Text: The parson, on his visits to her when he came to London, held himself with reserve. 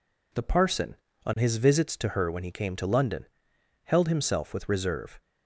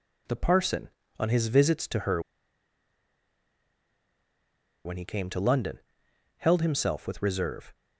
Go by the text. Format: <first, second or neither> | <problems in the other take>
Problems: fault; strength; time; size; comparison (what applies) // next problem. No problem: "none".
first | pauses between "her" and "when"; strong; at 2.1 s; 2.6 s long